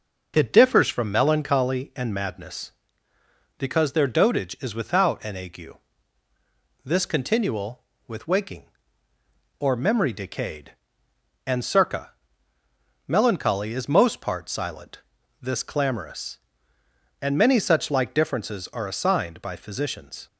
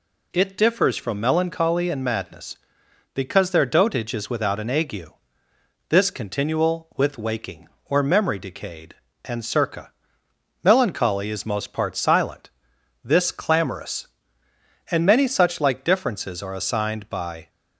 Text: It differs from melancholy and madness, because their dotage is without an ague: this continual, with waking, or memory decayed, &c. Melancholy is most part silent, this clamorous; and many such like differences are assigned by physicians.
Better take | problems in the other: first | stops before "physicians"; at 17.4 s

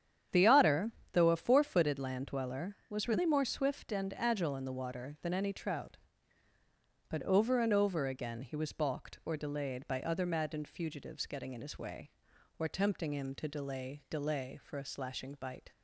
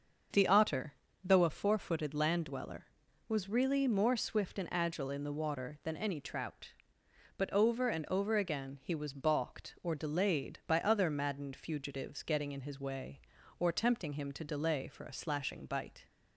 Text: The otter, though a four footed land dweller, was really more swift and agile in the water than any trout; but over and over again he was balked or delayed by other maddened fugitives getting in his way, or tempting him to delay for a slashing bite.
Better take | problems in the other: second | starts louder than the rest; strong; until 1.5 s; 9 dB; also in the second // says "delay" twice; at 14.1 s

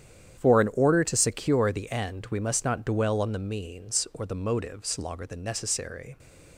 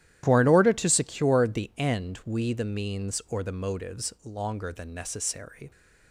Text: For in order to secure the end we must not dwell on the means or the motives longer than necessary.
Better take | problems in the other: first | starts louder than the rest; strong; until 1.2 s; 12.5 dB; strong in the first // skips "must not dwell on"; at 2.5 s

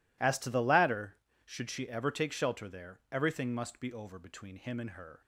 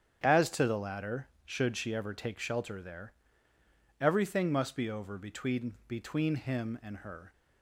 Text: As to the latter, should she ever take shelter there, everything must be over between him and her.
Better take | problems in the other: first | starts louder than the rest; strong; until 1.2 s; 8.5 dB // says "between" twice; at 5.8 s

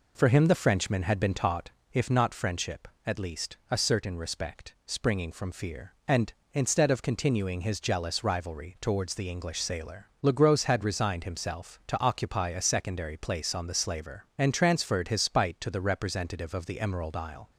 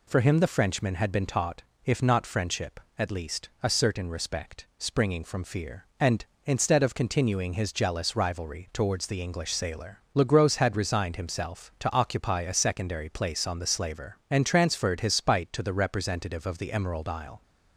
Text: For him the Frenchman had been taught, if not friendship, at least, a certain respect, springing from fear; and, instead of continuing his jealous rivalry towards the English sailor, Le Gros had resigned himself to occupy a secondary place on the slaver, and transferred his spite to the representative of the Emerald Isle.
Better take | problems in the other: second | starts louder than the rest; noticeable; until 1.9 s; 4 dB

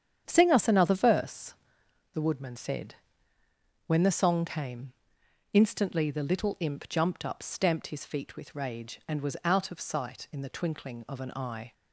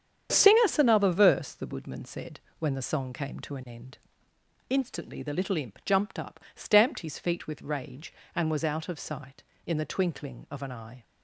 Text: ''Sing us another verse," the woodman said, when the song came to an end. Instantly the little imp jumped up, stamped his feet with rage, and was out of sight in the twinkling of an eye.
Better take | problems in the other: second | starts louder than the rest; strong; until 1.2 s; 8.5 dB; strong in the second // skips "to an end"; at 5.2 s

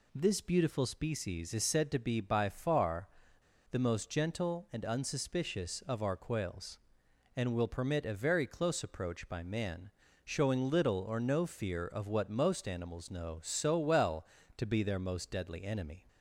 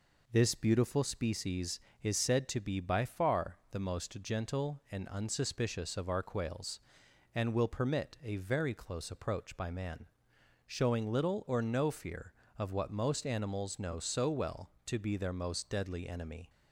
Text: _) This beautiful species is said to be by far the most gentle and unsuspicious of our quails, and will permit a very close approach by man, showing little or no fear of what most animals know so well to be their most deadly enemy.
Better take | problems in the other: second | pauses between "far" and "the"; noticeable; at 3.0 s; 0.63 s long

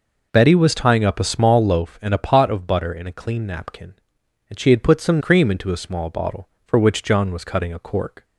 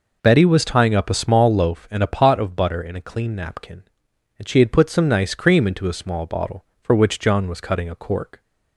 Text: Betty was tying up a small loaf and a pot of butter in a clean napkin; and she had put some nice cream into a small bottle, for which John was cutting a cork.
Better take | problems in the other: second | skips "nice"; at 5.1 s

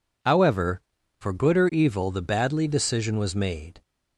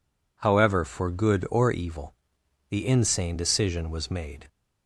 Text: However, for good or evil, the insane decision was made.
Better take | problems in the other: second | says "badly" for "insane"; at 2.2 s

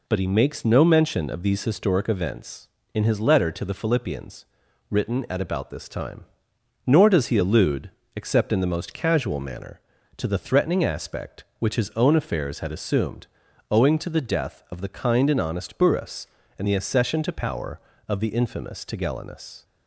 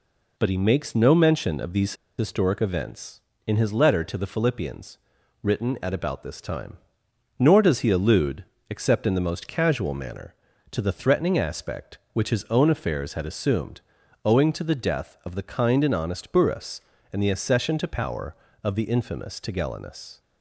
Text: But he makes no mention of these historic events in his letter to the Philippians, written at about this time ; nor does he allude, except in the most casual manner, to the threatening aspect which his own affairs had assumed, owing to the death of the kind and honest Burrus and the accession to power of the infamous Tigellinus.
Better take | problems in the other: first | pauses between "these" and "historic"; slight; at 1.9 s; 0.23 s long

